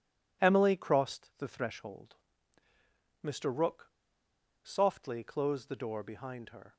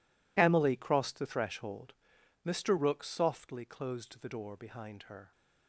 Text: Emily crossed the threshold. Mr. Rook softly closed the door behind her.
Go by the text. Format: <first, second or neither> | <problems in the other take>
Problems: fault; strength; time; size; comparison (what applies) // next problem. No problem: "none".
second | pauses between "Rook" and "softly"; noticeable; at 3.8 s; 0.74 s long